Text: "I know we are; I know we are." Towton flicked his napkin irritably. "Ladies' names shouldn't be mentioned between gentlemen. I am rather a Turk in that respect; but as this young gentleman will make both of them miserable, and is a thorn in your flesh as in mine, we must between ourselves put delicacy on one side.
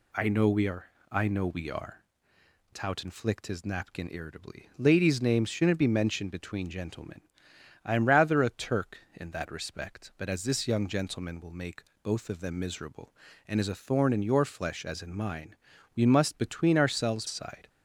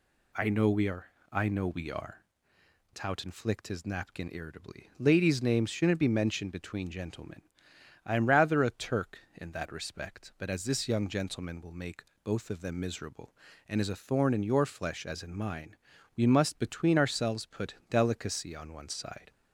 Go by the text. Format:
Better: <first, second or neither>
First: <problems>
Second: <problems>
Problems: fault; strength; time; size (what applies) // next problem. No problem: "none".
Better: second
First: pauses between "make" and "both"; slight; at 11.8 s; 0.22 s long // skips "put delicacy on one"; at 17.2 s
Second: pauses between "make" and "both"; slight; at 12.0 s; 0.22 s long